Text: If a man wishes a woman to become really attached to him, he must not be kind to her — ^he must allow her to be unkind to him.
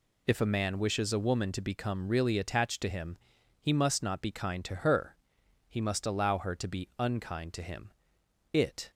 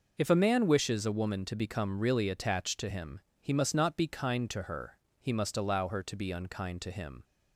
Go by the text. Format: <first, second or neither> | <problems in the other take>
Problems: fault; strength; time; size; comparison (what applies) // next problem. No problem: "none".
second | goes on to say "It"; slight; from 8.5 s on; 0.38 s long